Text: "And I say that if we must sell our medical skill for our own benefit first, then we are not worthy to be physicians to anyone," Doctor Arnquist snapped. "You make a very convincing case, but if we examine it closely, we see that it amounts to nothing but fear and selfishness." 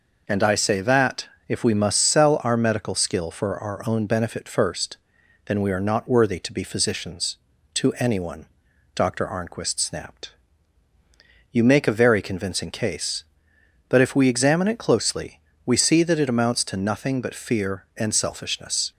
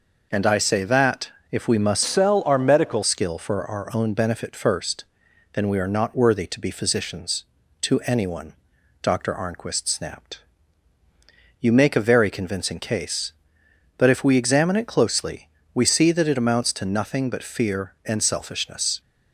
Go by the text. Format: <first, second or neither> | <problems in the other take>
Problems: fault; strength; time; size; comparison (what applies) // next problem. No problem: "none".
first | pauses between "that" and "if"; slight; at 1.3 s; 0.20 s long; slight in the first // changes voice from "sell" to "medical"; from 2.0 to 3.0 s; 1.0 s long